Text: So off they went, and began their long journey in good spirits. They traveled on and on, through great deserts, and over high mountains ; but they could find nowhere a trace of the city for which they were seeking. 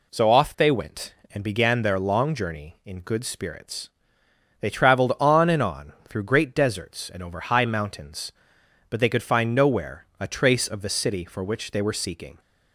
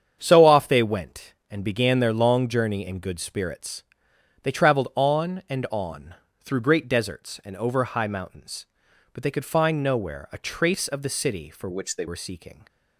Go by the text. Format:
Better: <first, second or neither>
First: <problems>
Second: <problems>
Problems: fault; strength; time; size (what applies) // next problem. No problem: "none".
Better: first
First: none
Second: starts louder than the rest; strong; until 1.2 s; 8 dB // changes voice from "which" to "they"; from 11.7 to 12.0 s; 0.3 s long